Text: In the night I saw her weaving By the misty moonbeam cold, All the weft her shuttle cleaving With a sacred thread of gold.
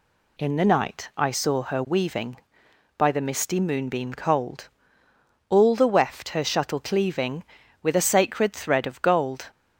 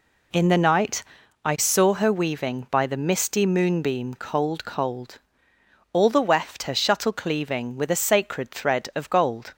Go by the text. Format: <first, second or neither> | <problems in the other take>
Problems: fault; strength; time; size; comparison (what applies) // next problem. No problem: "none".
first | pauses between "night" and "I"; at 1.0 s; 0.40 s long // says "cold" twice; at 4.6 s